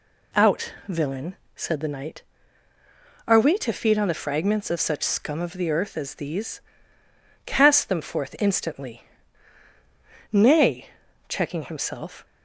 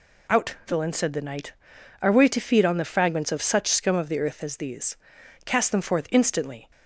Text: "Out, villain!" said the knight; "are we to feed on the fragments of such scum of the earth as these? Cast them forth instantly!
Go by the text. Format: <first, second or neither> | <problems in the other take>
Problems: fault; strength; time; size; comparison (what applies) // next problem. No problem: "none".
second | goes on to say "Nay checking himself"; strong; from 10.3 s on; 1.9 s long